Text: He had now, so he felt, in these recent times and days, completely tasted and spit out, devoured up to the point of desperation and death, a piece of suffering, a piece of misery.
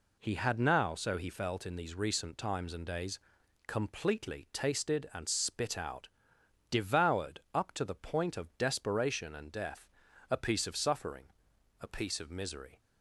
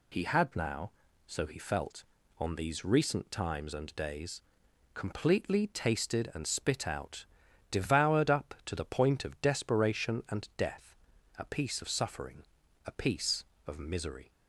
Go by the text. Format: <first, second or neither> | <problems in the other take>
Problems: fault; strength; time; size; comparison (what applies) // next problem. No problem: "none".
first | says "on" for "in"; at 2.3 s